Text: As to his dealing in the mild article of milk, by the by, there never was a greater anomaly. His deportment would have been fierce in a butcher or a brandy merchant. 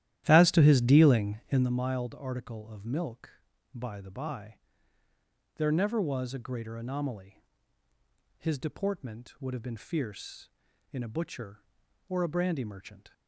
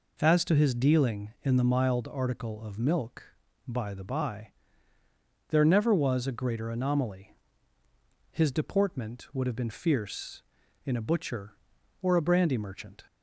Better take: second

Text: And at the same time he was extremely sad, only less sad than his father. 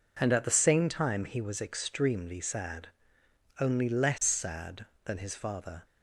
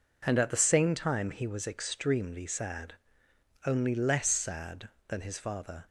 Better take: neither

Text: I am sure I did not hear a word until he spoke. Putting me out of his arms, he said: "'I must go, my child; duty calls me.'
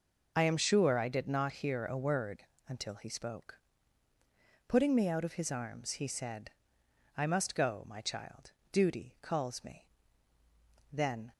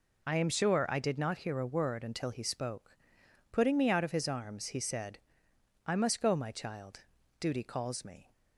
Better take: second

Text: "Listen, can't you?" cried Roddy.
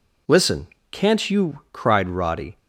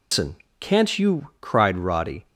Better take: first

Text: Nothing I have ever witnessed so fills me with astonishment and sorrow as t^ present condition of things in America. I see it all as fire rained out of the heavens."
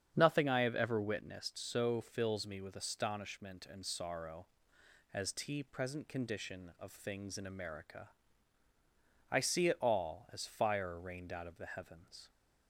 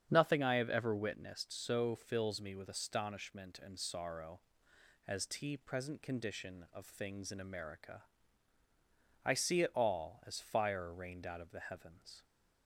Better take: neither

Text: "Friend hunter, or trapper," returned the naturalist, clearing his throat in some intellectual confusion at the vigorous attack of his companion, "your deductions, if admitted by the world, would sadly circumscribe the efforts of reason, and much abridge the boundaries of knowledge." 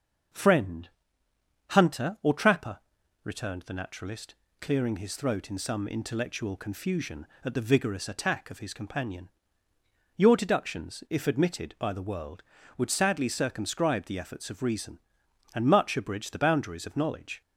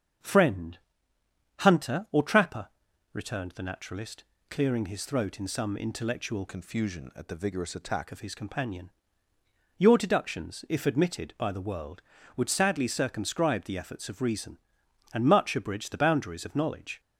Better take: first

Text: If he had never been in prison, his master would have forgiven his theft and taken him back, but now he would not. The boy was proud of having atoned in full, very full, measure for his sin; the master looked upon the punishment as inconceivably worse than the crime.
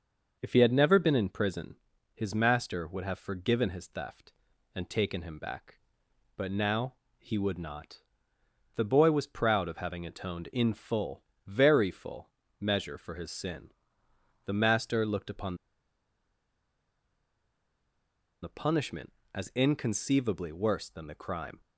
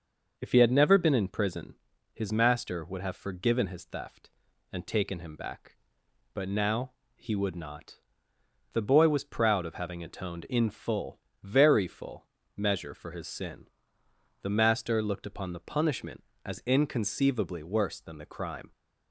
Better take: second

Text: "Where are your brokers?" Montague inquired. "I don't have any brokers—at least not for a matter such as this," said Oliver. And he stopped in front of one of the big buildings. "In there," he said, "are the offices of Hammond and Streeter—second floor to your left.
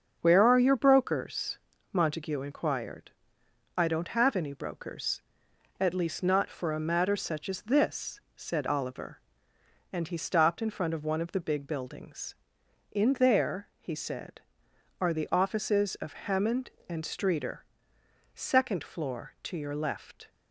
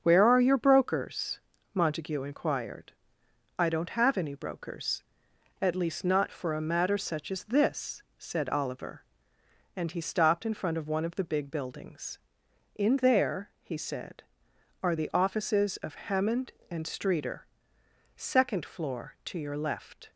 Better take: neither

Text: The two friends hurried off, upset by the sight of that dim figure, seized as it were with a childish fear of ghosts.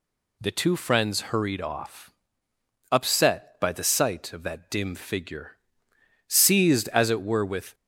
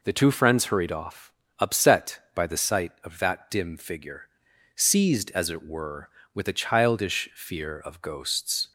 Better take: second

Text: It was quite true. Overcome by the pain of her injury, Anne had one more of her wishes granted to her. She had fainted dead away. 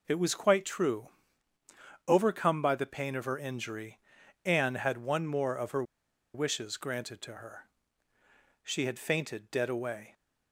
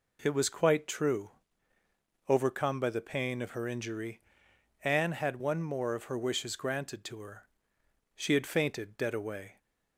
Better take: second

